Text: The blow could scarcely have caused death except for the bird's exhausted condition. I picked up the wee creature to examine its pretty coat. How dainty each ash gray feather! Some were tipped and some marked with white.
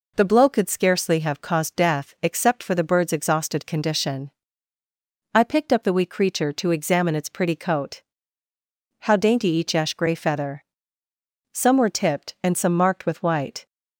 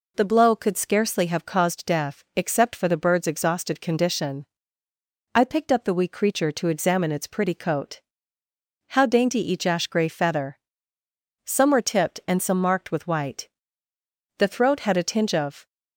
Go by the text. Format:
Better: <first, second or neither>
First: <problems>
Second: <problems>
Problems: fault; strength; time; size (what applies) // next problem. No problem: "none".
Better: first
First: none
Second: goes on to say "The throat had a tinge of"; noticeable; from 14.3 s on; 1.2 s long